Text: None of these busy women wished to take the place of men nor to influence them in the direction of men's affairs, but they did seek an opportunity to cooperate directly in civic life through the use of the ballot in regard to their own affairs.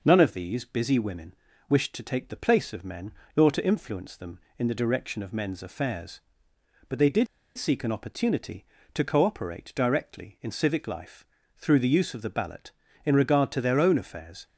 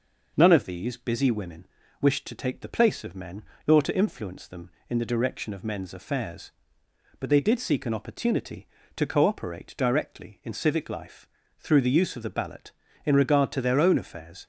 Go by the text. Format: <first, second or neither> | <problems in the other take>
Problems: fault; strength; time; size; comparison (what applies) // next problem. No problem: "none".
second | pauses between "women" and "wished"; slight; at 1.3 s; 0.34 s long; slight in the second // pauses between "men" and "nor"; slight; at 3.1 s; 0.26 s long; slight in the second // pauses between "did" and "seek"; slight; at 7.2 s; 0.31 s long // pauses between "life" and "through"; slight; at 11.2 s; 0.32 s long; slight in the second